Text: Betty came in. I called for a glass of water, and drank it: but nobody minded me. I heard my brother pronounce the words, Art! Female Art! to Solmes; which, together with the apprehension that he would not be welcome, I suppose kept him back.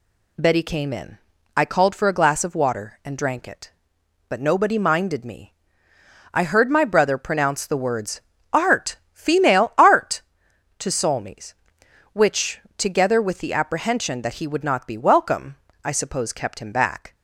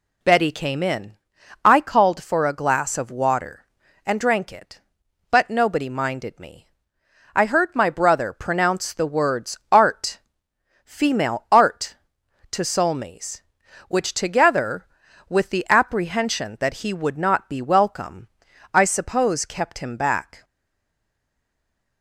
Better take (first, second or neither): first